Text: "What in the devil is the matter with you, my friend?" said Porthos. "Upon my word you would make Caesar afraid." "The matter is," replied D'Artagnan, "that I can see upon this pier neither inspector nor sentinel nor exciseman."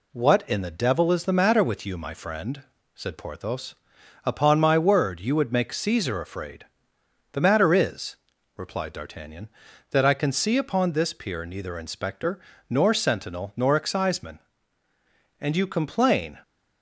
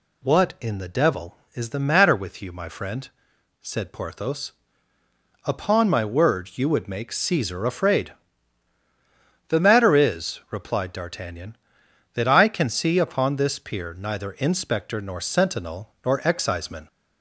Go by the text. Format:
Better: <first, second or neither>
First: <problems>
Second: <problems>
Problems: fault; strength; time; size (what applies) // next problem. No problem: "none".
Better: second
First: pauses between "inspector" and "nor"; slight; at 12.3 s; 0.28 s long // goes on to say "And you complain"; noticeable; from 15.3 s on; 1.0 s long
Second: none